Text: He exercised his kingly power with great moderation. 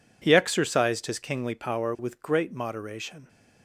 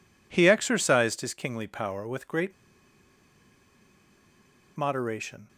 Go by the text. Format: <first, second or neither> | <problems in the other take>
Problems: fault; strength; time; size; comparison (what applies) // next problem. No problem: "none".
first | pauses between "great" and "moderation"; strong; at 2.5 s; 2.2 s long